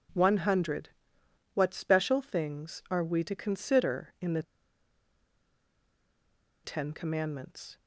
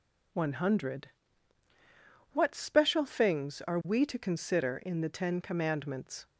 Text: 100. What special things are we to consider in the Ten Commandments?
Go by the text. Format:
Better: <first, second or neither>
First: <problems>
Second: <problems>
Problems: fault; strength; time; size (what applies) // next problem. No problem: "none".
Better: second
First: pauses between "the" and "Ten"; strong; at 4.4 s; 2.2 s long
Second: none